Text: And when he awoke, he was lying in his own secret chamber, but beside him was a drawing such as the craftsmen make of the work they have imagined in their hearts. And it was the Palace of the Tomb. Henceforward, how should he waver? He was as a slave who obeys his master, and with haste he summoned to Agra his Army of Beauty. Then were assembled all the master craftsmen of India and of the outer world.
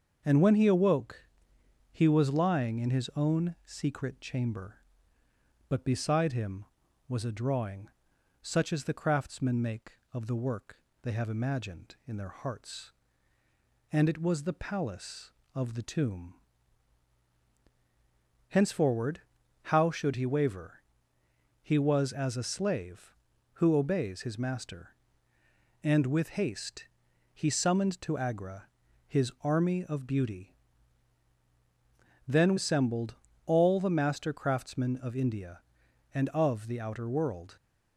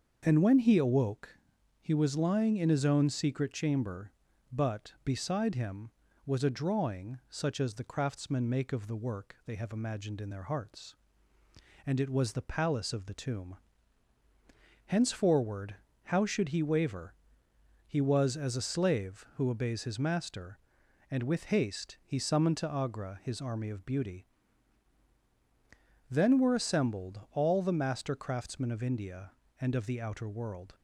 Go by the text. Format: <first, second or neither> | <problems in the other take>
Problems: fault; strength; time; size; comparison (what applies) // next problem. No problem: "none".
second | starts louder than the rest; until 1.2 s; 6.5 dB; also in the second // pauses between "drawing" and "such"; noticeable; at 7.8 s; 0.52 s long // pauses between "work" and "they"; slight; at 10.7 s; 0.26 s long // pauses between "haste" and "he"; noticeable; at 26.8 s; 0.48 s long // pauses between "Agra" and "his"; at 28.6 s; 0.38 s long // skips "were"; at 32.5 s // pauses between "assembled" and "all"; slight; at 33.1 s; 0.30 s long